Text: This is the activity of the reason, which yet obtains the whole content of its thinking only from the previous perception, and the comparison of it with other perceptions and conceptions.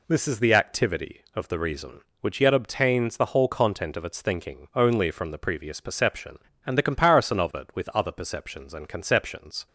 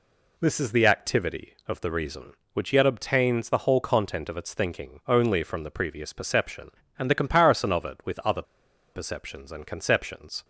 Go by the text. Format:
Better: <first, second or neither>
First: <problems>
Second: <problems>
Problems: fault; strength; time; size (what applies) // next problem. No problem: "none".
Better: first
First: none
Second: pauses between "other" and "perceptions"; noticeable; at 8.4 s; 0.50 s long